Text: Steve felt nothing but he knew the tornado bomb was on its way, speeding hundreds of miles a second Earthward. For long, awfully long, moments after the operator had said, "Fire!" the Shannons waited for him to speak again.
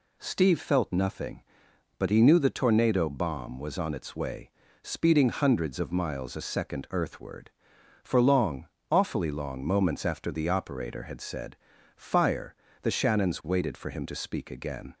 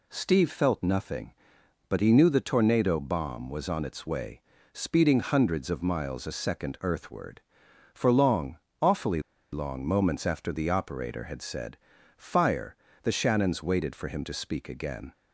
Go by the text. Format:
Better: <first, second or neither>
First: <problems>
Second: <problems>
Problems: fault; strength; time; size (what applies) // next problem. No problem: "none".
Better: first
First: none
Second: pauses between "awfully" and "long"; slight; at 9.2 s; 0.30 s long